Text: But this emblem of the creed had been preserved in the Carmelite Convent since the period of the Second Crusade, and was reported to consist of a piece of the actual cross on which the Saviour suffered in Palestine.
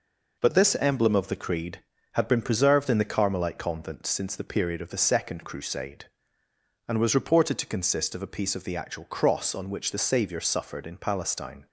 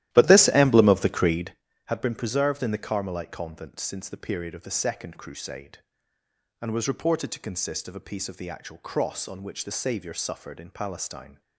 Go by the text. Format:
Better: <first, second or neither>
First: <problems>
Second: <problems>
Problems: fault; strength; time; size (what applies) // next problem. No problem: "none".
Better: first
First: none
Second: starts louder than the rest; strong; until 1.6 s; 14 dB